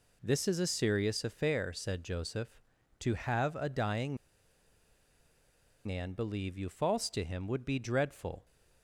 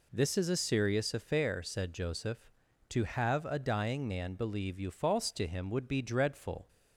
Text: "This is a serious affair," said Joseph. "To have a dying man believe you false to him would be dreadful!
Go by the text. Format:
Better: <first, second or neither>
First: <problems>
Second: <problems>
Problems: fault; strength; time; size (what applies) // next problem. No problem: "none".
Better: second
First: pauses between "dying" and "man"; strong; at 4.1 s; 1.6 s long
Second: none